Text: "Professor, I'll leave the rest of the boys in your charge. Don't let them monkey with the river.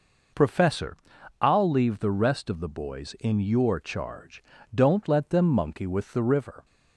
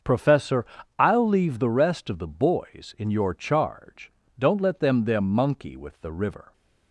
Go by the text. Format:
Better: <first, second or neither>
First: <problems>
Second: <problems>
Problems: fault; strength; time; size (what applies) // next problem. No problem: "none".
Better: first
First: none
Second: starts louder than the rest; until 1.3 s; 6.5 dB // says "them" twice; at 5.0 s